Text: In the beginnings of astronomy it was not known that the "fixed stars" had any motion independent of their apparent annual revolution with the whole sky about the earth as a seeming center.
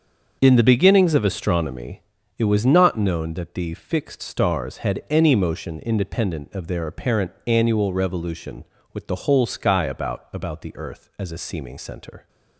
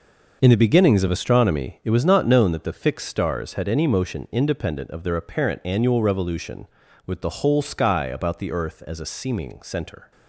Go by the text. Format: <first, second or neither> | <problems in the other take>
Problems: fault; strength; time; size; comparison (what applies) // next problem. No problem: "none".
second | starts louder than the rest; until 1.4 s; 6.5 dB // pauses between "astronomy" and "it"; slight; at 2.0 s; 0.36 s long // says "about" twice; at 10.3 s